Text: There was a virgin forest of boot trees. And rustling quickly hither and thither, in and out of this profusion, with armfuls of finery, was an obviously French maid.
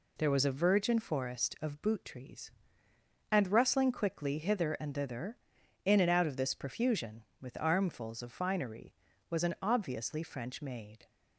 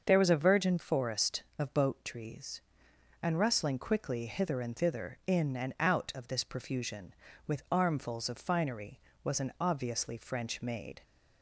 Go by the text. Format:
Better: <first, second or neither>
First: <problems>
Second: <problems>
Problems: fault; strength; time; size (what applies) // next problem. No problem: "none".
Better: first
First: none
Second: starts louder than the rest; until 1.0 s; 6.5 dB // says "boat" for "boot"; at 1.7 s